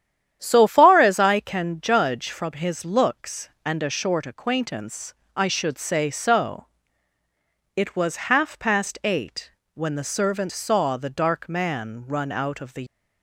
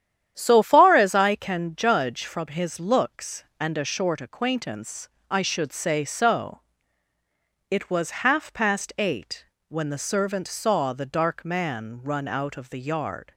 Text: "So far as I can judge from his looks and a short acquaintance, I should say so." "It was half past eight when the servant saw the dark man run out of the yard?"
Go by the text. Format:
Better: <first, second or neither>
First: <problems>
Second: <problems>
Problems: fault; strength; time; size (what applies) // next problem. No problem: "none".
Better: second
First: starts louder than the rest; strong; until 1.4 s; 10 dB // pauses between "eight" and "when"; slight; at 9.5 s; 0.22 s long // stops before "yard"; at 12.8 s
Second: starts louder than the rest; strong; until 1.3 s; 10 dB // pauses between "eight" and "when"; slight; at 9.4 s; 0.22 s long